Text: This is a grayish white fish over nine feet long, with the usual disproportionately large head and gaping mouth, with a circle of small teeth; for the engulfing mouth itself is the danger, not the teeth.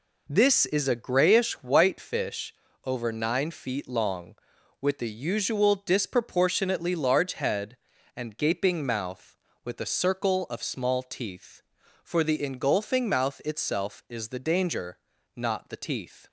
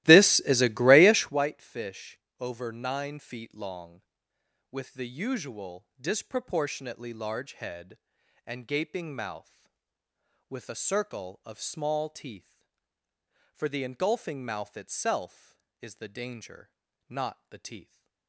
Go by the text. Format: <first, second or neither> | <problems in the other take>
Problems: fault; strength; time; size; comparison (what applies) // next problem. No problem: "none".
first | starts louder than the rest; strong; until 1.4 s; 16.5 dB // pauses between "fish" and "over"; slight; at 2.1 s; 0.22 s long; slight in the first